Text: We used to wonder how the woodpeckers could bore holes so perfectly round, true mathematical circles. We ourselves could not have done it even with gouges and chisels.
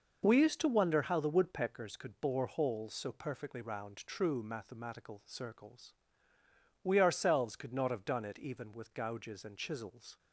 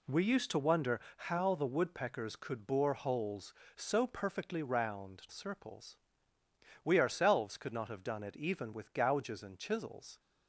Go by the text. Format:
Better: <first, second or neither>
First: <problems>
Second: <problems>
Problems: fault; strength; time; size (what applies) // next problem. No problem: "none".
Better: first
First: none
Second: pauses between "wonder" and "how"; slight; at 0.9 s; 0.16 s long // skips "true mathematical"; at 5.2 s